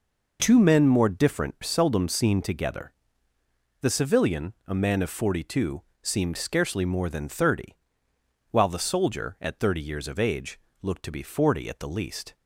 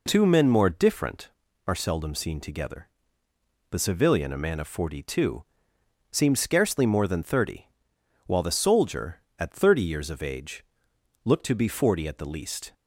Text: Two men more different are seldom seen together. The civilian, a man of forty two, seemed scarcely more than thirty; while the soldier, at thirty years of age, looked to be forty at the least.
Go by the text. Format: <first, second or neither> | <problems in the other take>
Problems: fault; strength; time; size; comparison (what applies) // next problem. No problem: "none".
second | skips "are"; at 1.5 s